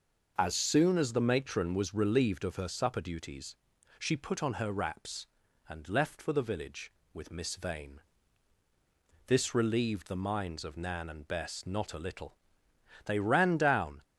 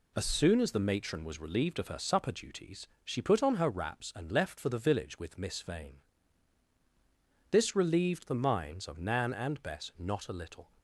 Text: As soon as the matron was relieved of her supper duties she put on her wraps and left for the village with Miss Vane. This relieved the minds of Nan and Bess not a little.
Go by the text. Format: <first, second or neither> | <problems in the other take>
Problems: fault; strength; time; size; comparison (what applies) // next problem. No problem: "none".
second | pauses between "duties" and "she"; at 3.5 s; 0.44 s long; slight in the second // goes on to say "They ran down"; noticeable; from 13.0 s on; 0.98 s long